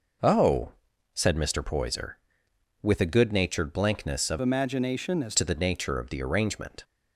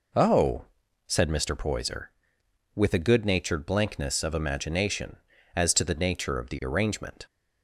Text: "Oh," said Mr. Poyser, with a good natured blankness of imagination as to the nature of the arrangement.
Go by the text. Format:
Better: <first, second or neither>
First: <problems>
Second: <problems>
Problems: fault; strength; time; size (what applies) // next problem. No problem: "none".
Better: second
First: changes voice from "imagination" to "as"; from 4.4 to 5.3 s; 0.9 s long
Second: none